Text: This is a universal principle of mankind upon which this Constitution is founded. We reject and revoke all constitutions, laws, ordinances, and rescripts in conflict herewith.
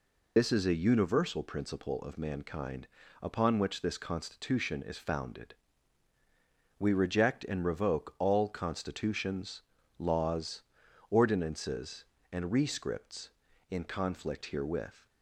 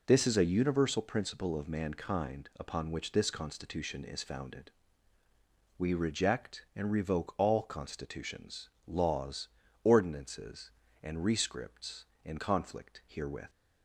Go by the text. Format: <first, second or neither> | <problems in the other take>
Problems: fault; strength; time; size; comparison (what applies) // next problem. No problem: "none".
second | loses the start of "This"; at 0.3 s; 50 ms // pauses between "mankind" and "upon"; slight; at 2.8 s; 0.32 s long